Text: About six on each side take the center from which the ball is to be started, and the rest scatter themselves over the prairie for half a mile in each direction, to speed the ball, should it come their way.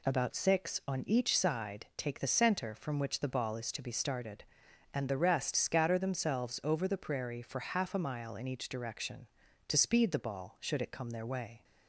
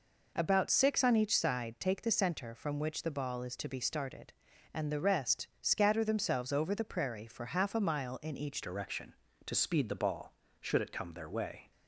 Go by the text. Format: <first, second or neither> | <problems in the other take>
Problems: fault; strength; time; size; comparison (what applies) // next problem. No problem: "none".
first | changes voice at "direction"; from 8.6 s on; 3.1 s long